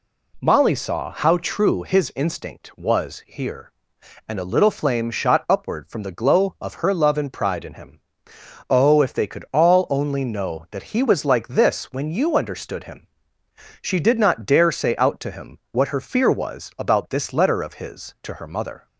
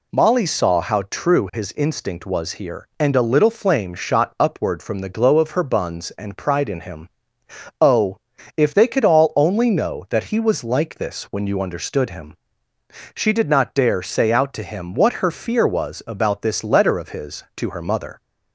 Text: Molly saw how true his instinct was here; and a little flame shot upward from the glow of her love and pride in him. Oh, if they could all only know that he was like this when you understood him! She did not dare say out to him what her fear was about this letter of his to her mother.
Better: first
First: none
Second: says "buns" for "love"; at 5.6 s

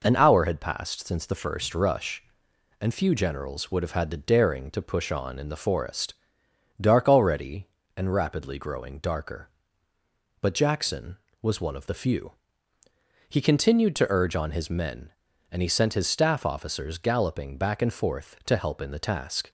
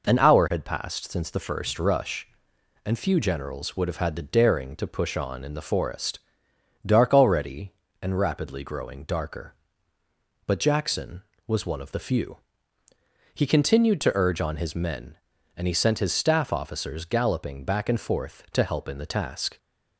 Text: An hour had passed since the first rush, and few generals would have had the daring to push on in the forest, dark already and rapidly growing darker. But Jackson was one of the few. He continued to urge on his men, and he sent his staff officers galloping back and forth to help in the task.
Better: neither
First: none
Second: none

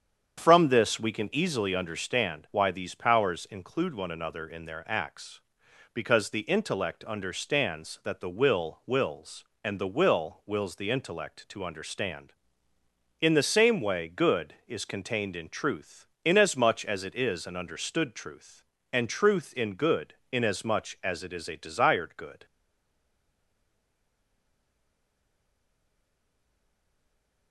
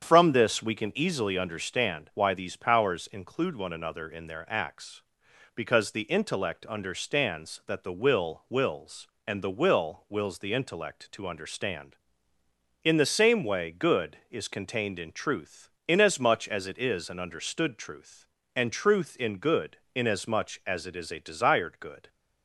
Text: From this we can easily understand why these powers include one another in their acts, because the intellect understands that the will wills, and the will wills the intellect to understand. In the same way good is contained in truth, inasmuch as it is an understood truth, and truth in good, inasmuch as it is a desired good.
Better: second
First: starts louder than the rest; strong; until 1.4 s; 8 dB // stays silent after the last word; strong; from 22.4 s on; 5.1 s long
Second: starts louder than the rest; strong; until 1.0 s; 8 dB

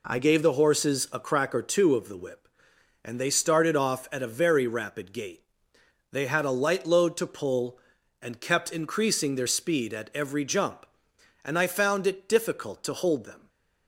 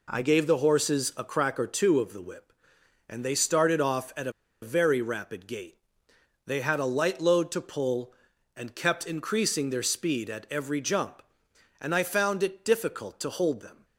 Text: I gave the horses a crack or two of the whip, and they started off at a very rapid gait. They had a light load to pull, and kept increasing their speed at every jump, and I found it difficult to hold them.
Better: first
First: none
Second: pauses between "a" and "very"; slight; at 4.3 s; 0.30 s long

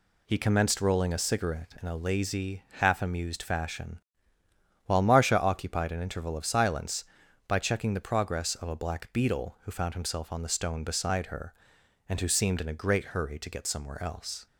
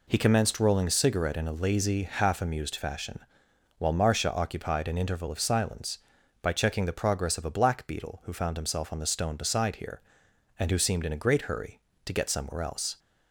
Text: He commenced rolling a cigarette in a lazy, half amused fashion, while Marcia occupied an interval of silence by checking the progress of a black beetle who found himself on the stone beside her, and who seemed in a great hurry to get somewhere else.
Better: first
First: none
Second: says "here" for "her"; at 9.7 s

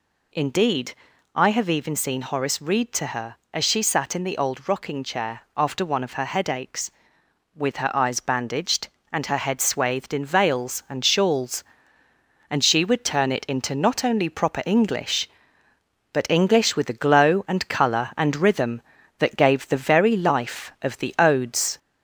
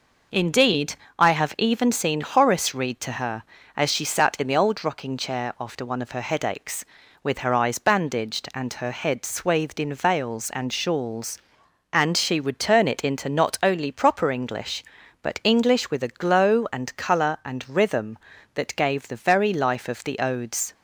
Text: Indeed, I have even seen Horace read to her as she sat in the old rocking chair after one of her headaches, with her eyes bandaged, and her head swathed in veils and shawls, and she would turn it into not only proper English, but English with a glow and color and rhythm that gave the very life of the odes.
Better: second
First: gets louder; slight; throughout; 2.5 dB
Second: none

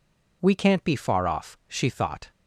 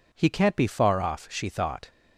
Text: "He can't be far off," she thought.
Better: second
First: says "We" for "He"; at 0.4 s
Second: none

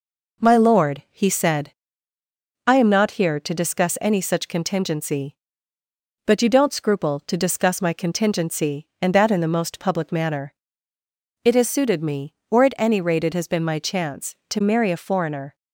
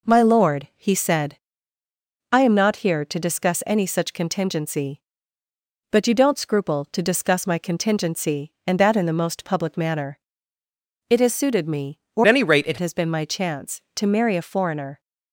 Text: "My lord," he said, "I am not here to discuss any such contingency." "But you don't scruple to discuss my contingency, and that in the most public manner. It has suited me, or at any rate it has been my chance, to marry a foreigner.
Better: first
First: none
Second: changes voice from "at" to "it"; from 12.2 to 12.7 s; 0.5 s long

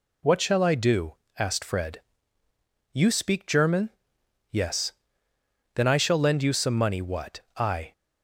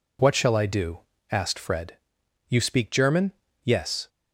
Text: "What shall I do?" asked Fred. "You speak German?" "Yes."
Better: second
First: goes on to say "Then I shall lend you some money what I"; strong; from 5.7 s on; 2.1 s long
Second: none

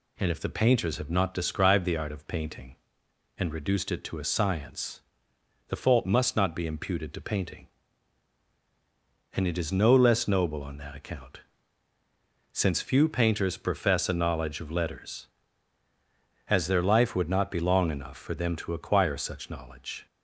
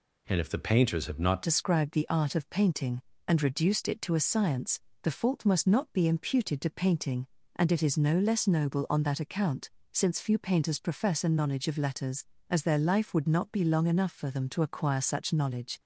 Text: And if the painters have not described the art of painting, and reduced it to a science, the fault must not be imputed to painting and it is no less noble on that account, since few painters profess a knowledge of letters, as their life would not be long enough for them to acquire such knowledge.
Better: first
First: none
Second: changes voice at "described"; from 1.4 s on; 14.3 s long

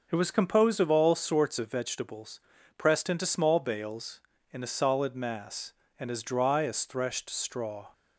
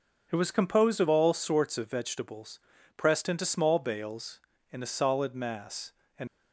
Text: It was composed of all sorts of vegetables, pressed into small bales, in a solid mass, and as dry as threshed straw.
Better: first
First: none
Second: stops before "as dry as threshed straw"; at 6.2 s

